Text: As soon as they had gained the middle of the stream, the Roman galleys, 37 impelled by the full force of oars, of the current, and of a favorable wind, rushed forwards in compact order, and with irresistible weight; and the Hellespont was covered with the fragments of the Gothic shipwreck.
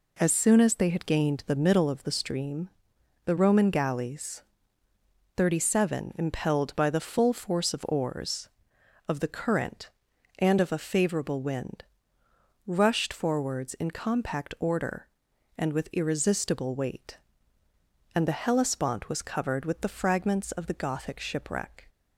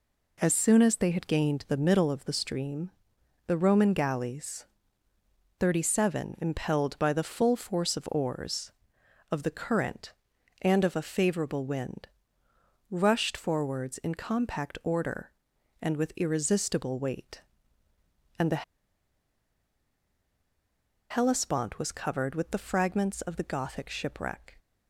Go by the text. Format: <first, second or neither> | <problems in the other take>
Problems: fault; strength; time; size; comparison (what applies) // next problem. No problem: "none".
first | pauses between "the" and "Hellespont"; strong; at 18.6 s; 2.4 s long